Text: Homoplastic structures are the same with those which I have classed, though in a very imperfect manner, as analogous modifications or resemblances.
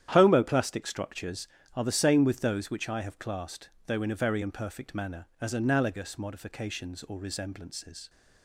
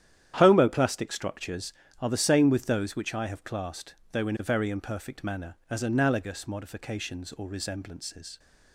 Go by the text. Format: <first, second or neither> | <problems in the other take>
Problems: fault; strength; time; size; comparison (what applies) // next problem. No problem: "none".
neither | starts louder than the rest; strong; the same in both